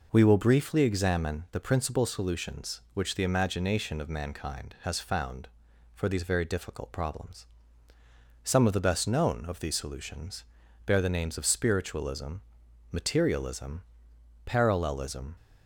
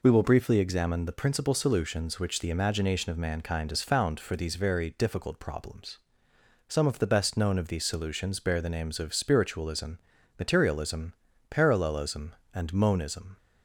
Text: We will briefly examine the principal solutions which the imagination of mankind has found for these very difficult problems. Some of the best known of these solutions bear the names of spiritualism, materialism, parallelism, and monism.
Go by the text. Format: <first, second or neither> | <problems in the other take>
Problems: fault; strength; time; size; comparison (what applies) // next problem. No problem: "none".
second | pauses between "solutions" and "bear"; at 10.4 s; 0.44 s long // stops before "and monism"; at 15.3 s